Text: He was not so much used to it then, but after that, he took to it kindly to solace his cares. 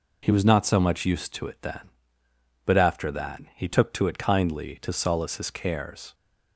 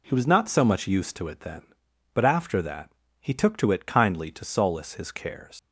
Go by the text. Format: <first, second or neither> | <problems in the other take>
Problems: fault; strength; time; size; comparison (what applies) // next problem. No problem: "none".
first | leaves "cares" unfinished; at 5.5 s; 115 ms